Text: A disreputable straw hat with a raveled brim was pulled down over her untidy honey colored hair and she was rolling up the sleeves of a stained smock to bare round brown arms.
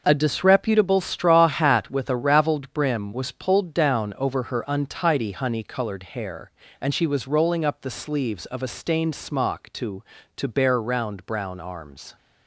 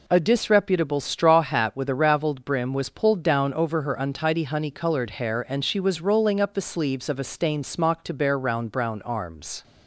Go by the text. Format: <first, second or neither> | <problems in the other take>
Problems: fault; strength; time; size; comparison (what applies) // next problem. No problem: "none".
second | says "to" twice; at 10.3 s